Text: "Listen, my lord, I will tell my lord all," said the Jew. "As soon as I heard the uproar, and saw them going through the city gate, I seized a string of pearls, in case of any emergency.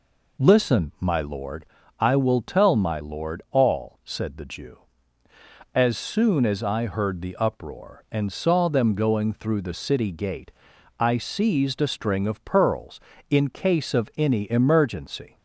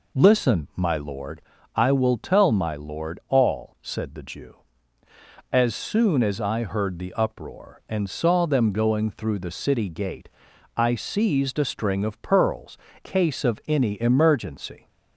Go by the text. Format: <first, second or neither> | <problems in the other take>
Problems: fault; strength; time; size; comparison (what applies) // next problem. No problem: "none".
first | skips "in"; at 12.9 s